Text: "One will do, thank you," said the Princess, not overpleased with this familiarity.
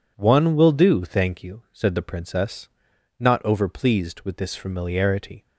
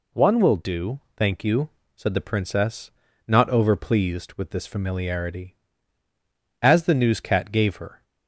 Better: first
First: none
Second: goes on to say "As the newscat gave her"; from 6.6 s on; 1.4 s long

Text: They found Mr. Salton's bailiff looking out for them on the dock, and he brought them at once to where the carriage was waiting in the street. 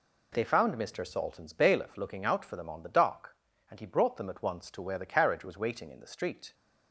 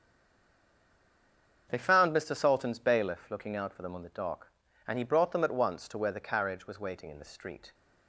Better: first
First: none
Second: stays silent before the first word; noticeable; until 1.6 s; 1.6 s long // starts louder than the rest; until 2.7 s; 6.5 dB

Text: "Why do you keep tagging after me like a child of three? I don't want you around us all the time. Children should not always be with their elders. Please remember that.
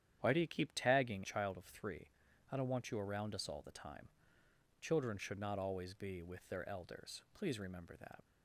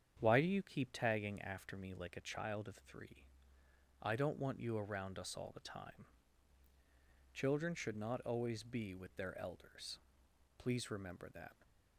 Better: second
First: starts louder than the rest; strong; until 1.2 s; 10 dB // skips "after me like a"; at 1.2 s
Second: starts louder than the rest; strong; until 1.2 s; 8 dB

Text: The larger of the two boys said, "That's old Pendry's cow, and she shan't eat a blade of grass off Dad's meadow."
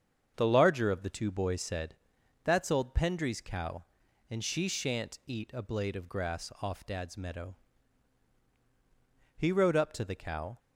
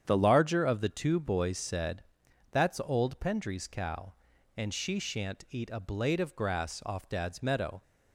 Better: second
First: starts louder than the rest; strong; until 1.3 s; 7 dB // goes on to say "He rode up to the cow"; noticeable; from 9.3 s on; 1.2 s long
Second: starts louder than the rest; strong; until 1.0 s; 8.5 dB

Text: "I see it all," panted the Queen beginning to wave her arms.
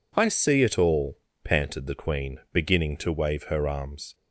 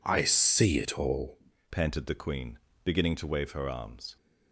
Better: first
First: none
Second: changes voice at "panted"; from 1.7 s on; 2.4 s long // pauses between "Queen" and "beginning"; slight; at 2.5 s; 0.24 s long

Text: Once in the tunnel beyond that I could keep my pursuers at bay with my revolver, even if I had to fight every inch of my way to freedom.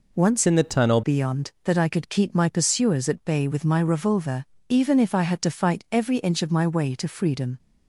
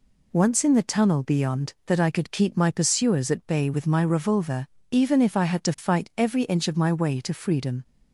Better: second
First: changes voice from "in" to "tunnel"; from 0.4 to 1.0 s; 0.6 s long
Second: none

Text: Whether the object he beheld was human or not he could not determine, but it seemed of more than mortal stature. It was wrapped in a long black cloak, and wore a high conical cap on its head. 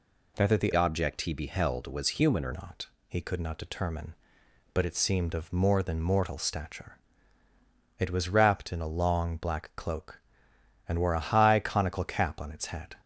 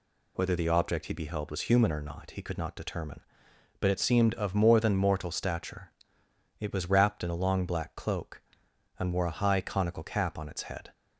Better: second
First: changes voice from "object" to "or"; from 0.7 to 2.5 s; 1.8 s long // pauses between "not" and "he"; slight; at 2.8 s; 0.20 s long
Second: none

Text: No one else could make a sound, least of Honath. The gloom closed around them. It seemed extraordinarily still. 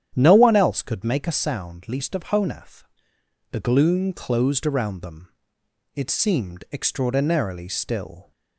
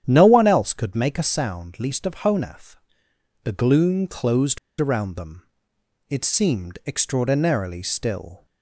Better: first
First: starts louder than the rest; strong; until 1.1 s; 10 dB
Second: starts louder than the rest; strong; until 1.0 s; 10 dB // pauses between "closed" and "around"; slight; at 4.5 s; 0.22 s long

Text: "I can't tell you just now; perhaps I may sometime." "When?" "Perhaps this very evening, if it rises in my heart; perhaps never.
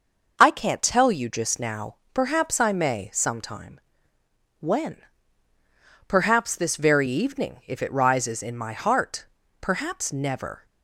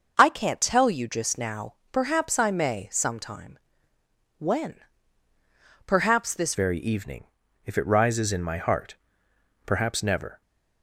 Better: first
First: none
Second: changes voice at "very"; from 6.5 s on; 3.9 s long

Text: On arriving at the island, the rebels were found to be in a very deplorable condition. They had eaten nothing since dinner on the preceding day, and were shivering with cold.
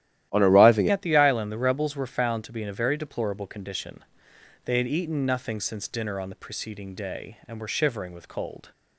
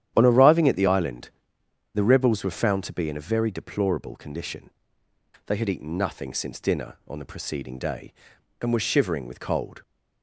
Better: second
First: starts louder than the rest; strong; until 1.3 s; 13 dB // changes voice at "at"; from 0.8 s on; 7.9 s long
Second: starts louder than the rest; strong; until 1.1 s; 10.5 dB

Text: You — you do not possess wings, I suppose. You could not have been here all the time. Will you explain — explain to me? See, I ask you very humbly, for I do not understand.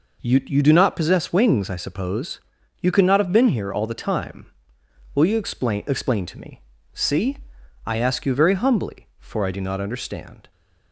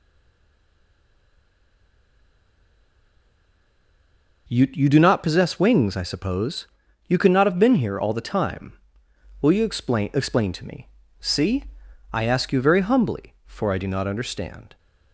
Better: first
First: none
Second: stays silent before the first word; strong; until 4.4 s; 4.4 s long

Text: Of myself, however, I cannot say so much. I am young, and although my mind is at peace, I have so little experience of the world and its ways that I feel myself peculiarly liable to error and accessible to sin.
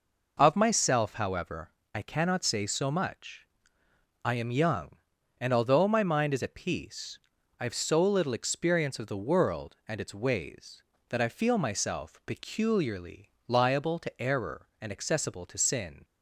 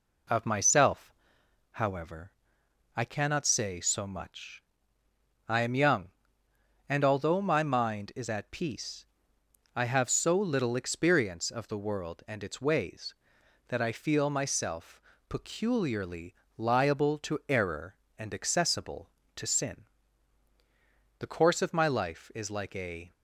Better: first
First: pauses between "peculiarly" and "liable"; slight; at 13.3 s; 0.18 s long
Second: pauses between "myself" and "peculiarly"; slight; at 15.0 s; 0.30 s long // pauses between "peculiarly" and "liable"; slight; at 16.3 s; 0.24 s long // goes on to say "The course of my life is like a"; strong; from 21.2 s on; 1.9 s long

